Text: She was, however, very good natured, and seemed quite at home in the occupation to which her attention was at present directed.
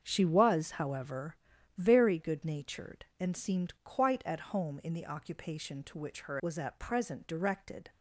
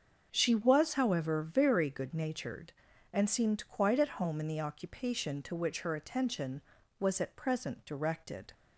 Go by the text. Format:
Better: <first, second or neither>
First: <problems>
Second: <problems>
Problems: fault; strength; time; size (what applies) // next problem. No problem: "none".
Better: second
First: starts louder than the rest; strong; until 1.0 s; 7 dB // skips "attention"; at 6.3 s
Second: starts louder than the rest; until 1.3 s; 6.5 dB